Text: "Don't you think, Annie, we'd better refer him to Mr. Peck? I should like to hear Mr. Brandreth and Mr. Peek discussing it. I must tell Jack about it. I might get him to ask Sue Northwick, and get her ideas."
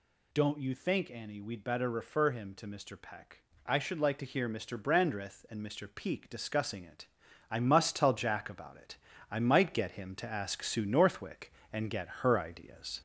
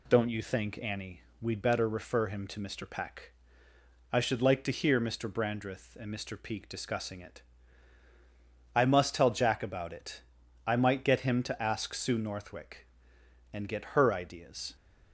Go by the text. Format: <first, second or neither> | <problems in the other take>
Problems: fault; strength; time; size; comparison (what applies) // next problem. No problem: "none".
second | gets louder; slight; throughout; 3 dB